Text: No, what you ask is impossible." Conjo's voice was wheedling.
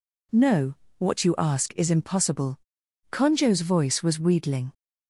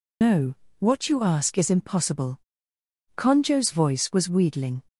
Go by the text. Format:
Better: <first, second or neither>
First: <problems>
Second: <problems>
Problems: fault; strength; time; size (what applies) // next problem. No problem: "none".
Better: first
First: none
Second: loses the start of "No"; at 0.2 s; 110 ms